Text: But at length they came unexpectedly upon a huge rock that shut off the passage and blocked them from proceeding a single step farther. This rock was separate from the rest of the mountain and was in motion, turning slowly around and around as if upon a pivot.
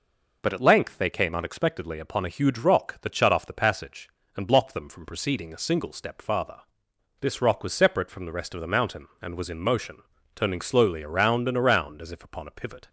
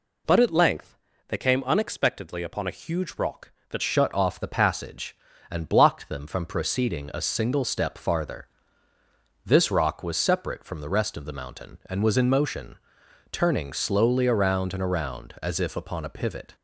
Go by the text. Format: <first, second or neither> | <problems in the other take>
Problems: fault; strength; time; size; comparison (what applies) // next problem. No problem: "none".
first | pauses between "length" and "they"; slight; at 0.9 s; 0.32 s long // changes voice at "shut"; from 3.8 s on; 12.7 s long